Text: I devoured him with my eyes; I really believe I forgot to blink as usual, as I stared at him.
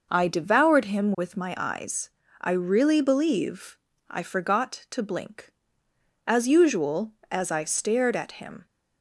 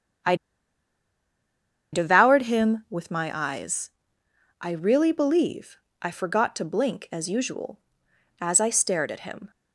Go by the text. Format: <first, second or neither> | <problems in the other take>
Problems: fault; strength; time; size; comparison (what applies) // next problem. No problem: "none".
first | starts louder than the rest; strong; until 2.8 s; 8.5 dB // pauses between "I" and "devoured"; strong; at 0.3 s; 1.5 s long // pauses between "believe" and "I"; slight; at 5.7 s; 0.24 s long; slight in the first